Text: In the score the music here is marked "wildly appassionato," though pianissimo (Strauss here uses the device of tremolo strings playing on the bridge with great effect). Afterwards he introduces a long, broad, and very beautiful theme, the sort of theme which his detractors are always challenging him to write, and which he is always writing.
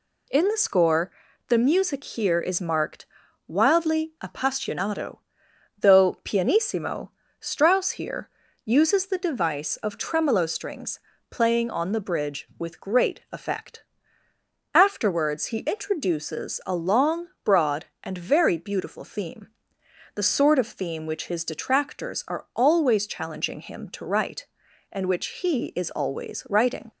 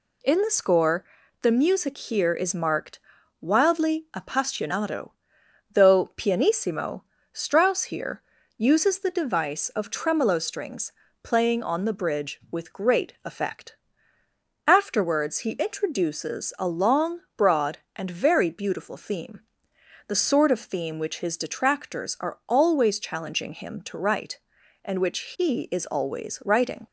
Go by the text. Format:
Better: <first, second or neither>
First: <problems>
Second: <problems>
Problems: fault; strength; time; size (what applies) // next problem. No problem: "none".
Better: neither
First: pauses between "score" and "the"; at 1.0 s; 0.38 s long // pauses between "marked" and "wildly"; at 3.0 s; 0.42 s long // pauses between "here" and "uses"; slight; at 8.2 s; 0.34 s long // pauses between "strings" and "playing"; slight; at 10.9 s; 0.32 s long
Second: pauses between "score" and "the"; at 1.0 s; 0.38 s long // pauses between "marked" and "wildly"; at 2.9 s; 0.42 s long // pauses between "here" and "uses"; slight; at 8.2 s; 0.34 s long // pauses between "strings" and "playing"; slight; at 10.9 s; 0.32 s long